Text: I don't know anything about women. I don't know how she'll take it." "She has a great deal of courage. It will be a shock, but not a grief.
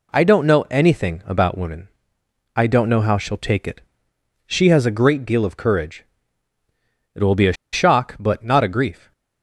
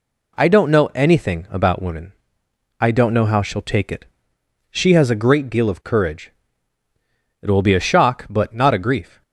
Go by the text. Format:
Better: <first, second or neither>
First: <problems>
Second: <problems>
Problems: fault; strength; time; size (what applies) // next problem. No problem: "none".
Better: second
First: pauses between "a" and "shock"; slight; at 7.5 s; 0.19 s long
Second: none